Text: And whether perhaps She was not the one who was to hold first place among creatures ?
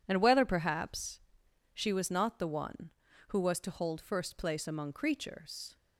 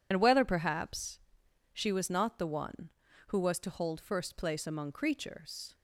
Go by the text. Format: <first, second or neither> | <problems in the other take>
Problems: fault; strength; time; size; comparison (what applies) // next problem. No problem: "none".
first | loses the start of "And"; at 0.1 s; 65 ms // pauses between "perhaps" and "She"; noticeable; at 1.1 s; 0.54 s long; noticeable in the first